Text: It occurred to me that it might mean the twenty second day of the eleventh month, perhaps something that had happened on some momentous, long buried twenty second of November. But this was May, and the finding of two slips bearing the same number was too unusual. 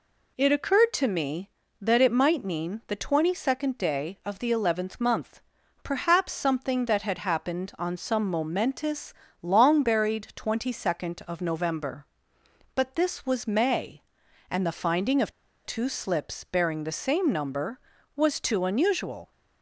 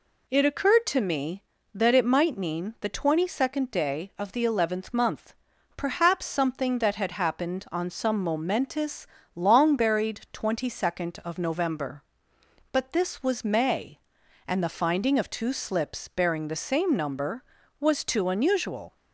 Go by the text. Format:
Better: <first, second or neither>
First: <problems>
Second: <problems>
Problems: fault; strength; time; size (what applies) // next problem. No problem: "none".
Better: second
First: pauses between "of" and "two"; slight; at 15.3 s; 0.33 s long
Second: none